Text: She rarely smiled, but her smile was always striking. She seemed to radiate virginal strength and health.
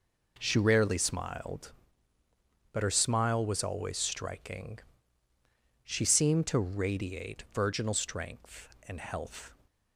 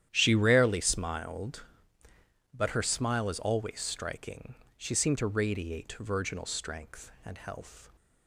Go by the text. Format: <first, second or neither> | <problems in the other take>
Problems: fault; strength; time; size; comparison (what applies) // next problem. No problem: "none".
first | starts louder than the rest; strong; until 1.1 s; 10.5 dB // says "is" for "was"; at 3.2 s